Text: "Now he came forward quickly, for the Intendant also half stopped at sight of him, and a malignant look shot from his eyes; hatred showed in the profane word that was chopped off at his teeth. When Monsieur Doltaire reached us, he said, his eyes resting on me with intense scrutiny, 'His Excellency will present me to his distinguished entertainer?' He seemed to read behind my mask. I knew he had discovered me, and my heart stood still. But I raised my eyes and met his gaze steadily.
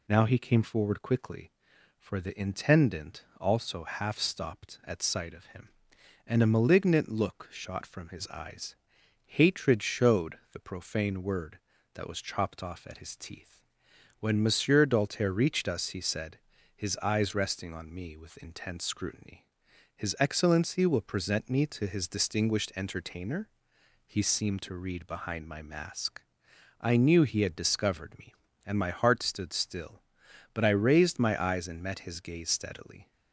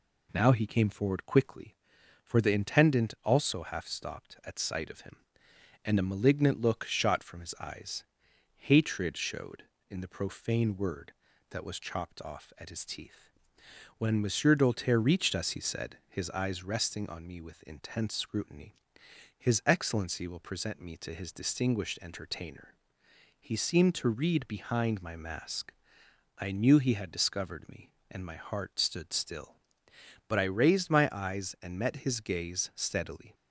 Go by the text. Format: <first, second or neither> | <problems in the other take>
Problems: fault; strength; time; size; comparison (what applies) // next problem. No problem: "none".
second | pauses between "Intendant" and "also"; slight; at 3.2 s; 0.16 s long // skips "in"; at 10.4 s